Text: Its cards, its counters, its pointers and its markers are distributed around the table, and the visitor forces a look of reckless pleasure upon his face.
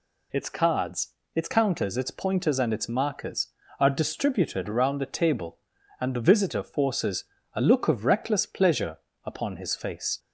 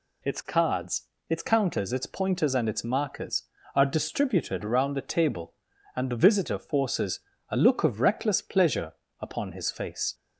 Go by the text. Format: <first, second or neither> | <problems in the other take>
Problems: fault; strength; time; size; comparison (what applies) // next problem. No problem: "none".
neither | pauses between "forces" and "a"; slight; the same in both // pauses between "pleasure" and "upon"; slight; the same in both